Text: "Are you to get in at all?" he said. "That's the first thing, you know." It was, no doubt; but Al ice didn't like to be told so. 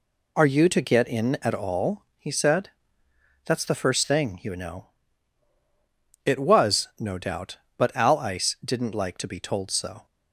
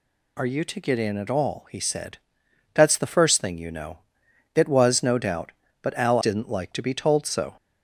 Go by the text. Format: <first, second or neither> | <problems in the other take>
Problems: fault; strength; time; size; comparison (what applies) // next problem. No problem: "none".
first | skips "ice"; at 6.1 s